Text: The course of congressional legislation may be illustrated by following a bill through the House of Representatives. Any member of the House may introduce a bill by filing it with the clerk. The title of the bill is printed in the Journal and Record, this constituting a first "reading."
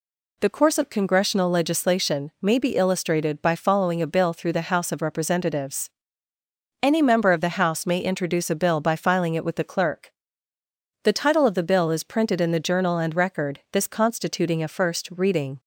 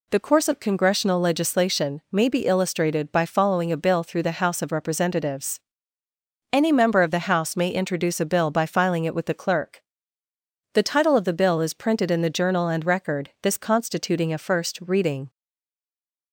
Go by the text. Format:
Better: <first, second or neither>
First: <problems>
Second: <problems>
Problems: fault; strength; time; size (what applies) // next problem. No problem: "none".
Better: first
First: none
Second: stays silent after the last word; from 15.2 s on; 1.1 s long